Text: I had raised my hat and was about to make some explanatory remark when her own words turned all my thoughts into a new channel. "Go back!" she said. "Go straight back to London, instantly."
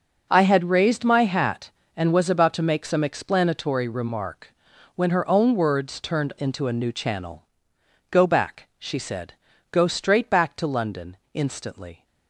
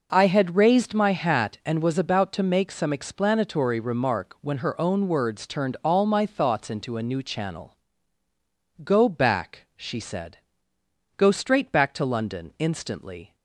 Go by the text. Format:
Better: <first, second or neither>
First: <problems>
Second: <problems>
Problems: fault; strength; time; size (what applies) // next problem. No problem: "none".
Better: second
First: pauses between "remark" and "when"; at 4.5 s; 0.44 s long // skips "all my thoughts"; at 6.3 s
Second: none